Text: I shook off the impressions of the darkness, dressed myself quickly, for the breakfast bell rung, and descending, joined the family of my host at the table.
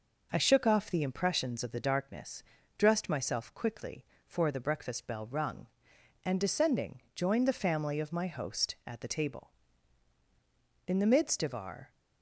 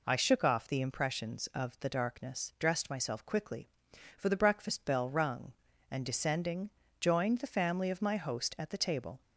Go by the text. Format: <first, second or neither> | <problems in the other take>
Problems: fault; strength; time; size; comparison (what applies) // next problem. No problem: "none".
second | goes on to say "In the midst of our"; noticeable; from 10.8 s on; 1.0 s long